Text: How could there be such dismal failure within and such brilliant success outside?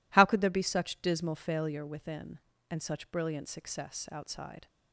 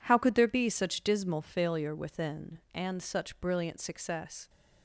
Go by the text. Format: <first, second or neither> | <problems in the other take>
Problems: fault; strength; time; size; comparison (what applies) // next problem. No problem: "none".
first | stops before "outside"; at 4.4 s